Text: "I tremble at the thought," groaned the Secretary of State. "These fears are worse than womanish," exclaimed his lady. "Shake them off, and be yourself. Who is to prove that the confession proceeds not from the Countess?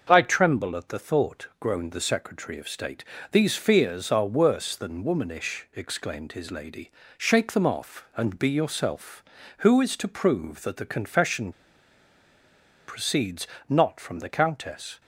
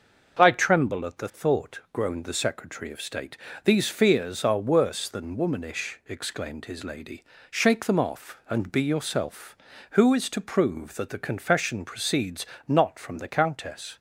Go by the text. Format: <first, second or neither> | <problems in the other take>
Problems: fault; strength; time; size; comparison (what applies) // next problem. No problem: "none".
second | starts louder than the rest; until 1.1 s; 6.5 dB; also in the second // pauses between "confession" and "proceeds"; strong; at 11.5 s; 1.3 s long // pauses between "proceeds" and "not"; slight; at 13.4 s; 0.20 s long; slight in the second